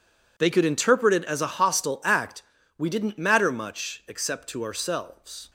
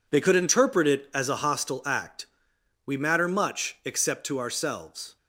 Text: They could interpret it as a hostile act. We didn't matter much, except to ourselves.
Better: first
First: none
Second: skips "didn't"; at 2.9 s

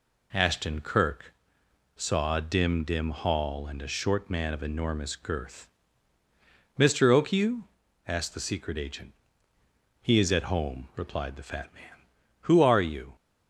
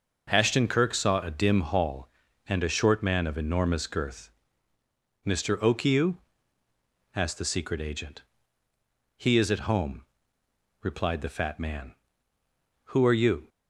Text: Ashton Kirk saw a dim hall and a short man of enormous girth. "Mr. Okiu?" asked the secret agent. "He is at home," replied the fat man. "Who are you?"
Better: second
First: pauses between "Kirk" and "saw"; noticeable; at 1.3 s; 0.64 s long // says "dim" twice; at 2.8 s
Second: none

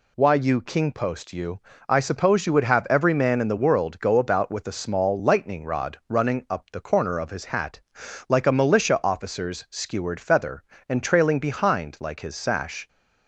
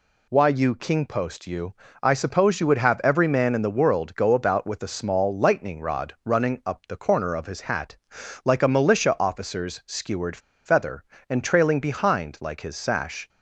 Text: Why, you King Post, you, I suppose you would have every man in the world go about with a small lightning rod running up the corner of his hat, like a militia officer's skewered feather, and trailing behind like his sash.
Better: first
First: none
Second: pauses between "skewered" and "feather"; slight; at 10.3 s; 0.27 s long

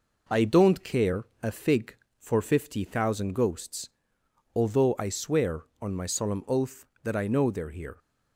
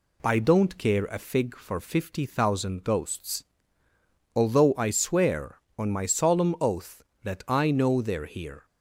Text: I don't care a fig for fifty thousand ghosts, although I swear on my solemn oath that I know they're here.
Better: second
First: gets quieter; slight; throughout; 2 dB // pauses between "care" and "a"; slight; at 1.2 s; 0.16 s long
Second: none

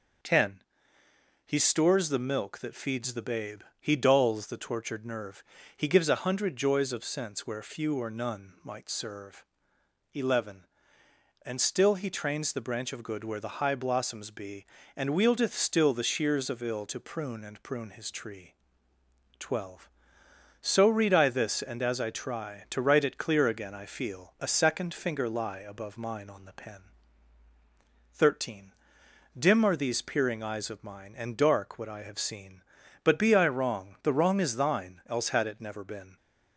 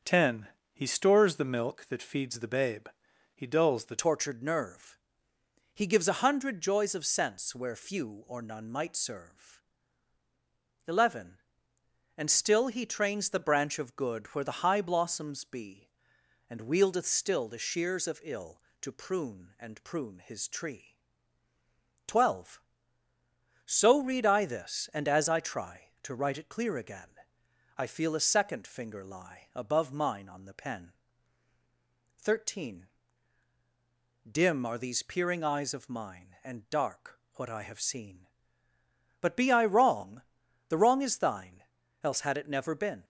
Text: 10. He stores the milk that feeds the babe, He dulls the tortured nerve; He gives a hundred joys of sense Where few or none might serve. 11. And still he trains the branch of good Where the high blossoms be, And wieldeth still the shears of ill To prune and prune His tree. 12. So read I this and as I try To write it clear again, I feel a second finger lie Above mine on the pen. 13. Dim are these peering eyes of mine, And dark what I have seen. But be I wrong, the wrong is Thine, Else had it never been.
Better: first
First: none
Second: starts louder than the rest; until 1.2 s; 6.5 dB // changes voice at "tortured"; from 3.9 s on; 39.1 s long // pauses between "dark" and "what"; slight; at 37.1 s; 0.18 s long

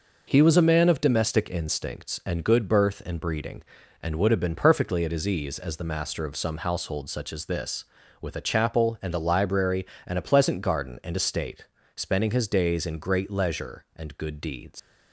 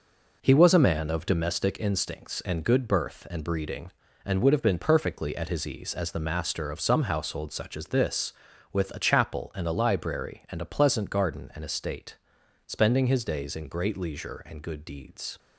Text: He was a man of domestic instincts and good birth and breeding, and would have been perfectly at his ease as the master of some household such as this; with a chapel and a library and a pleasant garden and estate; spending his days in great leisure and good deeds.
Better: second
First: leaves "deeds" unfinished; at 14.7 s; 105 ms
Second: none

